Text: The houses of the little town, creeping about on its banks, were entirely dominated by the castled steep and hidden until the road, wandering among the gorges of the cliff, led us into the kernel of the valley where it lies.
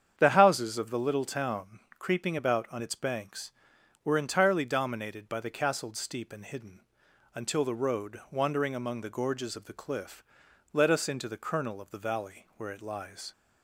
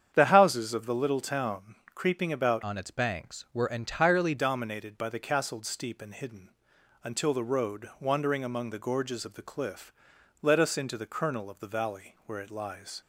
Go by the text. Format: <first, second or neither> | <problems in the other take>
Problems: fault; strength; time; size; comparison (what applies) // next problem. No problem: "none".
first | starts louder than the rest; strong; until 1.1 s; 8.5 dB; strong in the first // changes voice from "on" to "entirely"; from 2.6 to 4.3 s; 1.7 s long // pauses between "hidden" and "until"; noticeable; at 6.5 s; 0.52 s long; noticeable in the first